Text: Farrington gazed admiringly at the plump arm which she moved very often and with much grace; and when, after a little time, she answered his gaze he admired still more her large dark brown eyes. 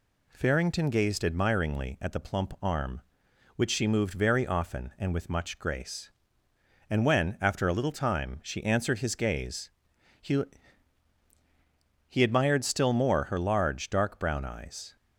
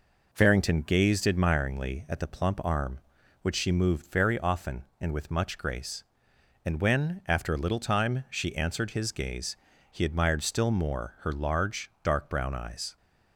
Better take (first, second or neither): second